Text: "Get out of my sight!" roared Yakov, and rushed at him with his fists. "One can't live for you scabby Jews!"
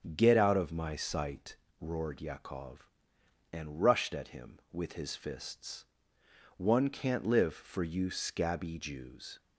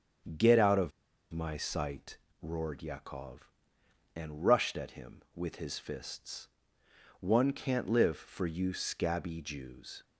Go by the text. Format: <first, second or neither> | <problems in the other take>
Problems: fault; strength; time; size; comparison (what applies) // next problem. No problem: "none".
first | starts louder than the rest; strong; until 1.7 s; 7.5 dB; strong in the first // pauses between "of" and "my"; at 0.9 s; 0.40 s long